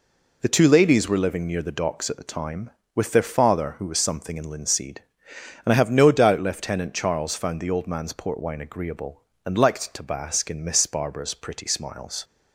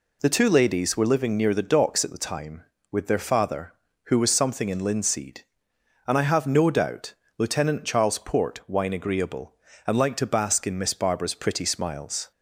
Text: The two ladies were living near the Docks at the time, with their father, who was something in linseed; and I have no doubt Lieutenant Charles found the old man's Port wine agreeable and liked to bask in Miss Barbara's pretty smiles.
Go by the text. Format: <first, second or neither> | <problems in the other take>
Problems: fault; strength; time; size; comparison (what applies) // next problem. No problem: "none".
first | pauses between "doubt" and "Lieutenant"; slight; at 7.1 s; 0.24 s long // skips "found the old man's"; at 8.1 s